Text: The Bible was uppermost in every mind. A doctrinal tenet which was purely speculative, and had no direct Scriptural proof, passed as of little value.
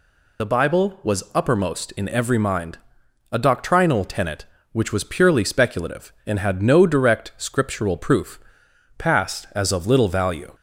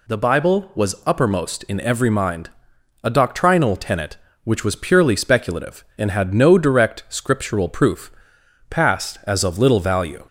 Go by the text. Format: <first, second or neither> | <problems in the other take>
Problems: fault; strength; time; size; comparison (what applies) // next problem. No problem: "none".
second | loses the start of "The"; at 0.3 s; 35 ms